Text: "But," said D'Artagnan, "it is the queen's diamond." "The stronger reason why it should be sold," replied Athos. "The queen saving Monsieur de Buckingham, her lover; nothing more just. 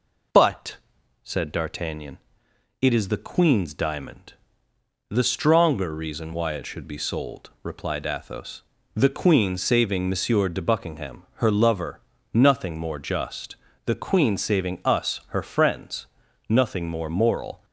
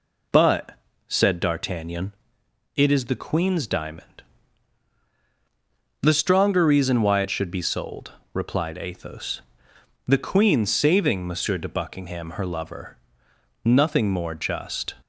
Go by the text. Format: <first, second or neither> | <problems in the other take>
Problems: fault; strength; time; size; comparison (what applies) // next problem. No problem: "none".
second | goes on to say "The queen saving us her friends nothing more moral"; strong; from 13.8 s on; 3.7 s long